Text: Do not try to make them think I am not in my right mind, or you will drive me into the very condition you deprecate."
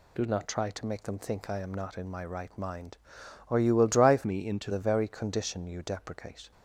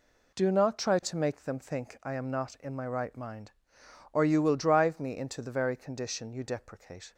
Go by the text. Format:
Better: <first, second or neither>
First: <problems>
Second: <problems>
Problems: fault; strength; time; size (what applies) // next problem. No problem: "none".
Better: second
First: changes voice from "me" to "into"; from 4.2 to 4.6 s; 0.4 s long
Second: none